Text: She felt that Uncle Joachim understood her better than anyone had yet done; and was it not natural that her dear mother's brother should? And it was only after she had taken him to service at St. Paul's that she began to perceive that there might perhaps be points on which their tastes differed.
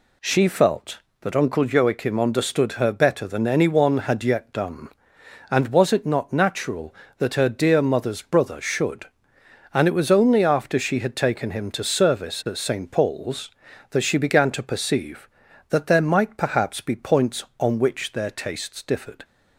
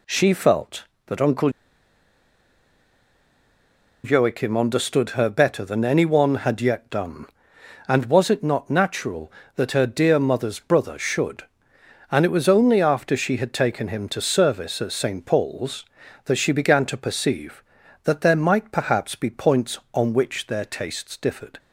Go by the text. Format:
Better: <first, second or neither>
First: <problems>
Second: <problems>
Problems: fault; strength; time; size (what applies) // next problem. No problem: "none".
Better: first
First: none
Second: pauses between "Uncle" and "Joachim"; strong; at 1.5 s; 2.5 s long